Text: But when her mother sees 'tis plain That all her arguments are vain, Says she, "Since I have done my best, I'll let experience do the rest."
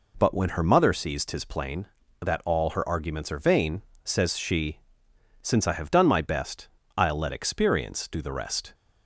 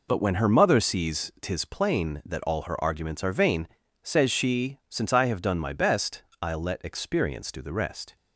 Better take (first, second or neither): neither